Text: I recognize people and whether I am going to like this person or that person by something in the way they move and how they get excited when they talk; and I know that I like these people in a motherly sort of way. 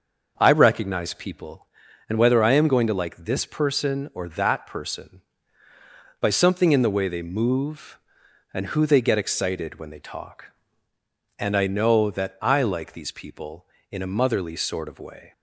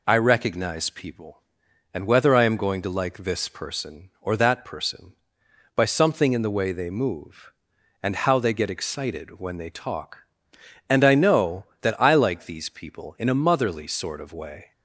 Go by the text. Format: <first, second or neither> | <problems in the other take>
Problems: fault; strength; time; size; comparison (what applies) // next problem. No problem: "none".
second | starts louder than the rest; until 1.3 s; 6 dB // says "who" for "how"; at 8.6 s